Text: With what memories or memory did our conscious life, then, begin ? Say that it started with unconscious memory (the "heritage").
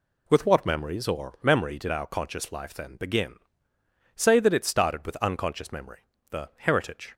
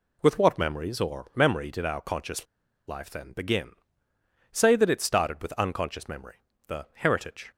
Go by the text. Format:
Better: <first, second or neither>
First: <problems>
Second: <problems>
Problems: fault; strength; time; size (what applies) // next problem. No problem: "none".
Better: first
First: none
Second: pauses between "conscious" and "life"; at 2.4 s; 0.42 s long